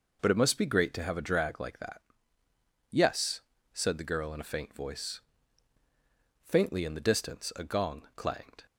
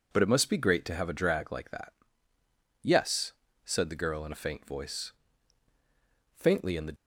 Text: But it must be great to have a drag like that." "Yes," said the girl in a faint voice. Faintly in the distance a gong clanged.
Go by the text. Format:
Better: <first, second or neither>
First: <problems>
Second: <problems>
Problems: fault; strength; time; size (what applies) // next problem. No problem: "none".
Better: first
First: none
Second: stops before "distance a gong clanged"; at 6.9 s